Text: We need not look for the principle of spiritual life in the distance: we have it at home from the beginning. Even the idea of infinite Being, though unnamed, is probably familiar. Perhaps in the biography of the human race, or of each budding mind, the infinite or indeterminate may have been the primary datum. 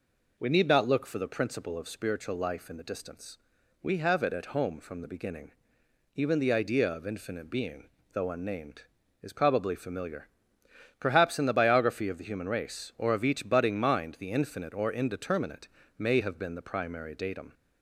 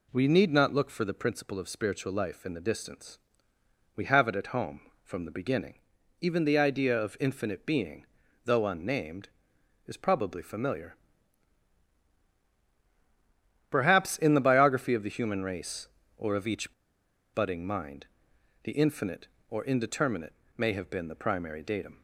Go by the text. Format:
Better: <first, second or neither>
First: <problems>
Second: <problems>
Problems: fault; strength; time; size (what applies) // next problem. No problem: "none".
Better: first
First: pauses between "indeterminate" and "may"; slight; at 15.6 s; 0.28 s long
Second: pauses between "each" and "budding"; noticeable; at 16.7 s; 0.61 s long // pauses between "indeterminate" and "may"; slight; at 20.3 s; 0.22 s long